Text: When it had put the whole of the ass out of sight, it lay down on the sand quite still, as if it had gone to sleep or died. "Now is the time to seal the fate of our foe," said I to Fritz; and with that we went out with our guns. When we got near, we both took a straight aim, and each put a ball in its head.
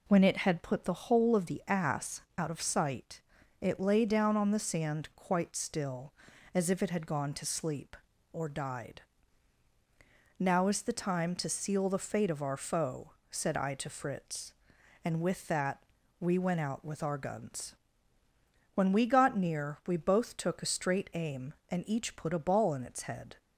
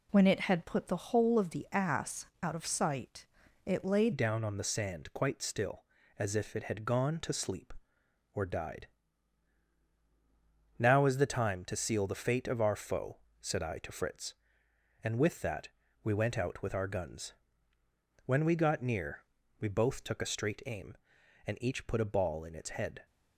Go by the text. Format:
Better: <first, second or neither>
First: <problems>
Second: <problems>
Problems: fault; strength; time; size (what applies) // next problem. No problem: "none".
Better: first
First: pauses between "ass" and "out"; slight; at 2.2 s; 0.16 s long // pauses between "that" and "we"; at 15.8 s; 0.38 s long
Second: pauses between "ass" and "out"; slight; at 2.2 s; 0.16 s long // changes voice at "down"; from 4.1 s on; 18.9 s long // pauses between "that" and "we"; slight; at 15.6 s; 0.34 s long